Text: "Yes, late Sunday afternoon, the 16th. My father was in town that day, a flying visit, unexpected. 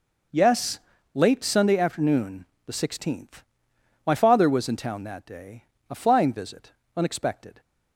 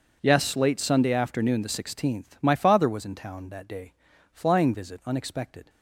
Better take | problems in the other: first | skips "a"; at 4.1 s

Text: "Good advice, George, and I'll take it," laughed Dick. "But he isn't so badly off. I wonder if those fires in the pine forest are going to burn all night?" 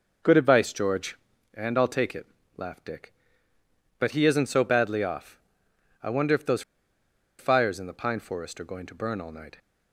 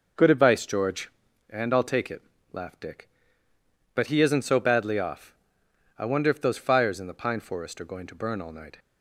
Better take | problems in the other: second | pauses between "those" and "fires"; noticeable; at 6.6 s; 0.77 s long

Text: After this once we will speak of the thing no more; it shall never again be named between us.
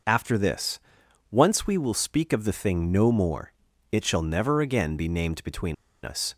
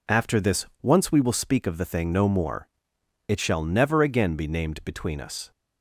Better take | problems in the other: second | pauses between "this" and "once"; noticeable; at 0.7 s; 0.50 s long; slight in the second // pauses between "between" and "us"; slight; at 5.7 s; 0.30 s long

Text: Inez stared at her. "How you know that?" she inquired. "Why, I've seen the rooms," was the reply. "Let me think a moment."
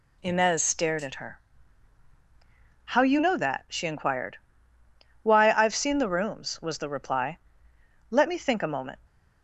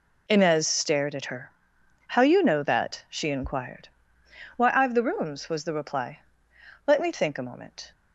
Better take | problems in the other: first | skips "seen"; at 4.9 s

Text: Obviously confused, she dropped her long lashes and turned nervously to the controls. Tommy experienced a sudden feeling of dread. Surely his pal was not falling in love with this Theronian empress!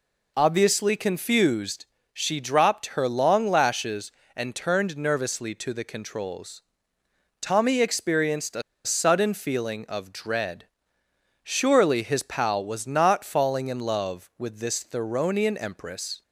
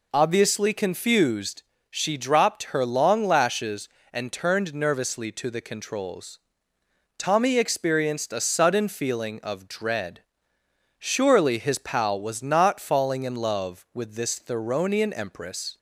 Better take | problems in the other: second | pauses between "a" and "sudden"; slight; at 8.6 s; 0.23 s long

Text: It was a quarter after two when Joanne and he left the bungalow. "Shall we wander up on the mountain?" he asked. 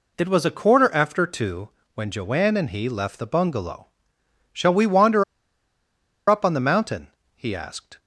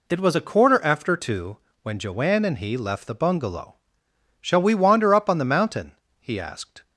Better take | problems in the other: second | pauses between "two" and "when"; slight; at 1.6 s; 0.26 s long; slight in the second // pauses between "wander" and "up"; at 5.2 s; 1.0 s long

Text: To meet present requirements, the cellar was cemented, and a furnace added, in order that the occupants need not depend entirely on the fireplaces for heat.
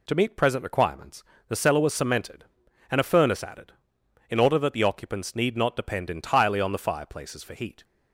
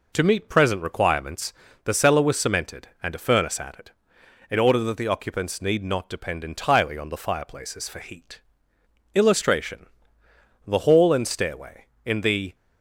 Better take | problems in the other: first | goes on to say "Illustration The Hall and Stairway In the"; strong; from 9.1 s on; 3.4 s long

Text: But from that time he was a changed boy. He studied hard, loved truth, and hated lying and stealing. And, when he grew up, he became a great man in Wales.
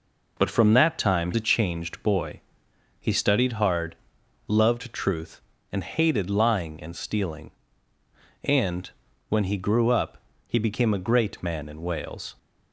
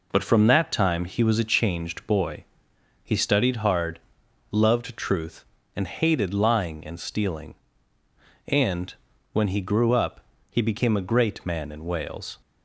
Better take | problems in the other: second | skips "he was"; at 1.3 s

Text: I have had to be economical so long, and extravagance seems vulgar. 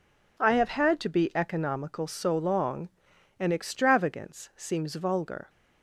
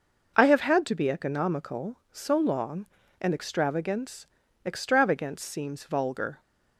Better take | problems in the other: first | says "extravagance" twice; at 4.6 s

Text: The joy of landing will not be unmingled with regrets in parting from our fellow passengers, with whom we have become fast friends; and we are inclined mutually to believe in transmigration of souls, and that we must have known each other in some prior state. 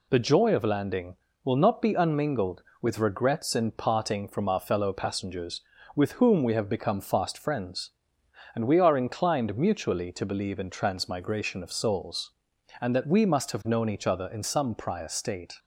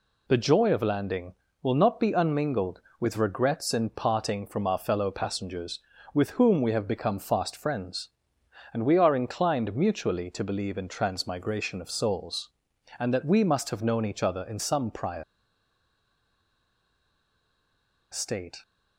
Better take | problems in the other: first | pauses between "prior" and "state"; strong; at 15.2 s; 2.8 s long

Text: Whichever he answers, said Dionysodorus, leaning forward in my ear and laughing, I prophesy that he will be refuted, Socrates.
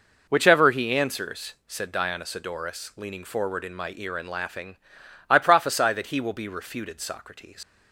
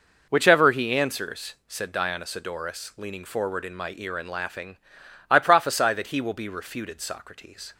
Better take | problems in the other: second | leaves "Socrates" unfinished; at 7.6 s; 95 ms

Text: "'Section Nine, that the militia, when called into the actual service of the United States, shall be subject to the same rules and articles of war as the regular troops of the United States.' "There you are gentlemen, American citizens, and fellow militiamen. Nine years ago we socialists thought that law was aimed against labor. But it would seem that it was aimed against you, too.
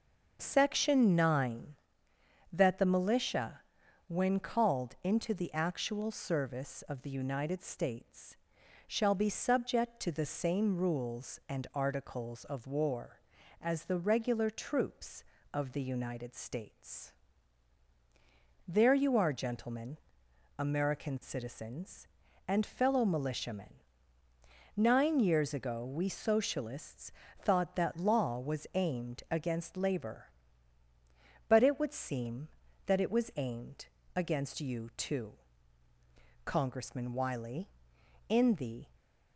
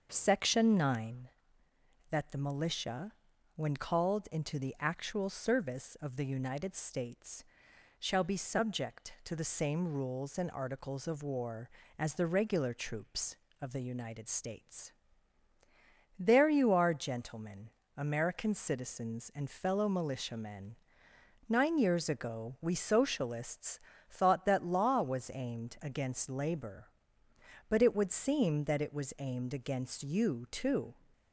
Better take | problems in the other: second | starts louder than the rest; until 1.4 s; 6.5 dB; also in the second // pauses between "socialists" and "thought"; slight; at 27.1 s; 0.28 s long; slight in the second // pauses between "aimed" and "against"; slight; at 33.8 s; 0.28 s long // goes on to say "Congressman Wiley in the"; strong; from 36.4 s on; 2.4 s long

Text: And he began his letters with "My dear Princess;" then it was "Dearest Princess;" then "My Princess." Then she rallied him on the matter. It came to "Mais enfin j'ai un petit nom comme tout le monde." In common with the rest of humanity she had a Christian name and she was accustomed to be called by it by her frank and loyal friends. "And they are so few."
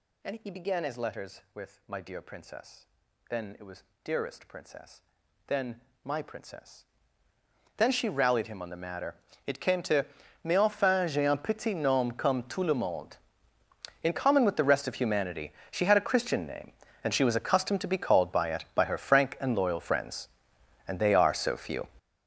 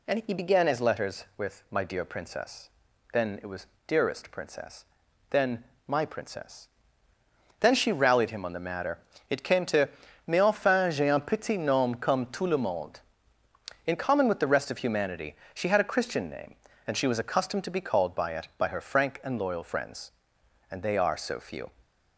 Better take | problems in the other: second | gets louder; strong; throughout; 13.5 dB // pauses between "was" and "Dearest"; slight; at 3.8 s; 0.20 s long; slight in the second // pauses between "then" and "My"; slight; at 5.7 s; 0.24 s long; slight in the second // pauses between "to" and "Mais"; at 10.0 s; 0.40 s long; also in the second // pauses between "humanity" and "she"; slight; at 15.5 s; 0.18 s long; slight in the second

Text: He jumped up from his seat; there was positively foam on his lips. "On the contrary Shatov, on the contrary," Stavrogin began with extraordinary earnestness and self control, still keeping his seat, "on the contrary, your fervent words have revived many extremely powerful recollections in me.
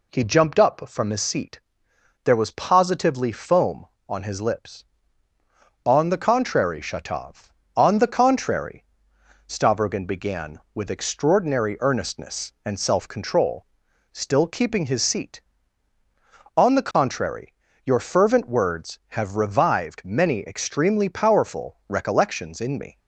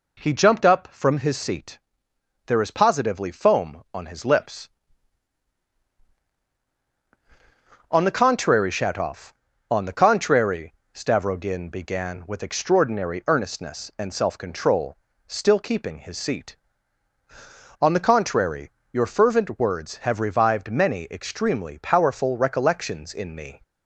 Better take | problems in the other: first | says "is" for "was"; at 2.6 s

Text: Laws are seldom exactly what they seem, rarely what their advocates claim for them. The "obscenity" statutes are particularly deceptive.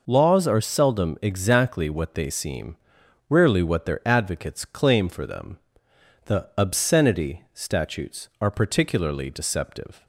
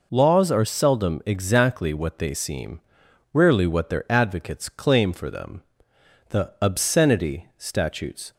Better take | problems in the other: first | stops before "are particularly deceptive"; at 8.3 s

